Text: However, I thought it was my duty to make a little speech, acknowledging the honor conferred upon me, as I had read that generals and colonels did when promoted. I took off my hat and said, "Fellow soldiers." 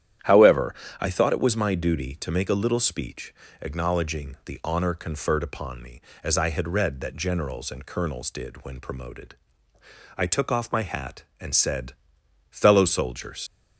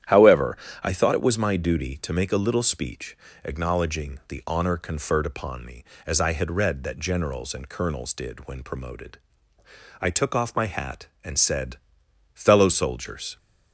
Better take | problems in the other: second | starts louder than the rest; strong; until 1.5 s; 10.5 dB; strong in the second // leaves "soldiers" unfinished; at 13.4 s; 65 ms

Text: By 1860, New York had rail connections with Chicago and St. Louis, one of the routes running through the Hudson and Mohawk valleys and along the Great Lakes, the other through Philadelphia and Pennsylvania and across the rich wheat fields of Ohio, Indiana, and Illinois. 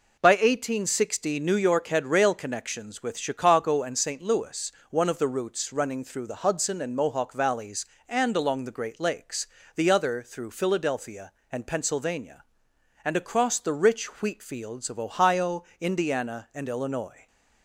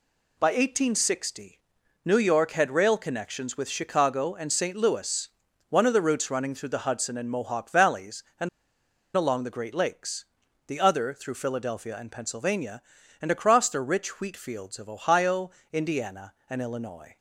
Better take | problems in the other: first | pauses between "and" and "along"; noticeable; at 8.4 s; 0.67 s long

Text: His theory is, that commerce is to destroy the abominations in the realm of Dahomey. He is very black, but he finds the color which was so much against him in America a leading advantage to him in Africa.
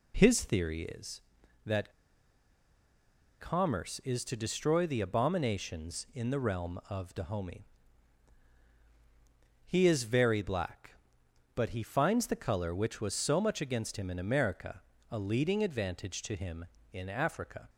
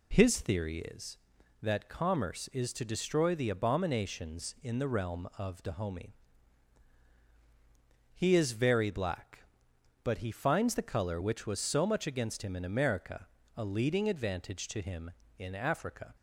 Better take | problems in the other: second | pauses between "that" and "commerce"; strong; at 1.9 s; 1.4 s long // pauses between "America" and "a"; slight; at 14.8 s; 0.28 s long; slight in the second

